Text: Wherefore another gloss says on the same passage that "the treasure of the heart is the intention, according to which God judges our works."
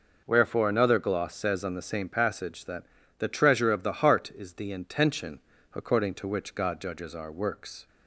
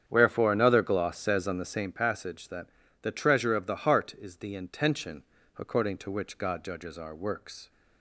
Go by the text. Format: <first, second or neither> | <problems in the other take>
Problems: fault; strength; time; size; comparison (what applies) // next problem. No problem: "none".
first | starts louder than the rest; strong; until 1.9 s; 8.5 dB // pauses between "that" and "the"; slight; at 2.6 s; 0.34 s long; slight in the first